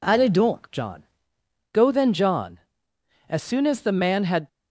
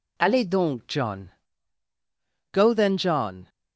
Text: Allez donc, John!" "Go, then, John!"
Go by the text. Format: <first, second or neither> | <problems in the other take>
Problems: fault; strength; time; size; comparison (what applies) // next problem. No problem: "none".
second | goes on to say "As soon as the man had"; noticeable; from 3.2 s on; 1.1 s long